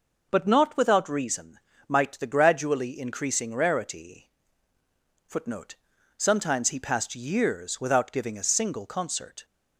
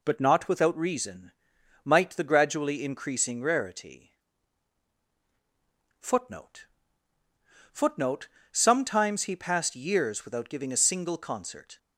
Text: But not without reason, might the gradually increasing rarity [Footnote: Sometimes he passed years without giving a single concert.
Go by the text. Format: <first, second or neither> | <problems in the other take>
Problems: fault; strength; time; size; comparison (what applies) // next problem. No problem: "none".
first | pauses between "rarity" and "Footnote"; strong; at 4.1 s; 1.8 s long; also in the first // says "Footnote" twice; at 7.7 s